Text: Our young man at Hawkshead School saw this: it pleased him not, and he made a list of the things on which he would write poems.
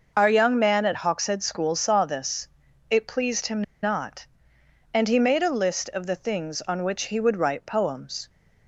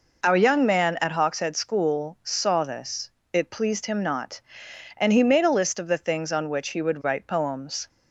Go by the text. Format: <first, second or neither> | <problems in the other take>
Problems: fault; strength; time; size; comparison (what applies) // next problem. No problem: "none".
second | pauses between "him" and "not"; slight; at 3.6 s; 0.19 s long